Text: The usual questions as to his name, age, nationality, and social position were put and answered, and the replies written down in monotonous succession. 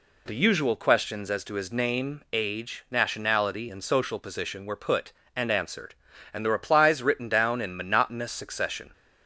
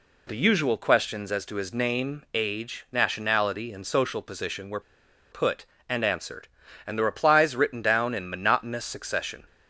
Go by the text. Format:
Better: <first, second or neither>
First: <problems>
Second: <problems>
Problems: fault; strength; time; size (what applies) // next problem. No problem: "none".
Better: first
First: none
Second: pauses between "were" and "put"; noticeable; at 4.8 s; 0.51 s long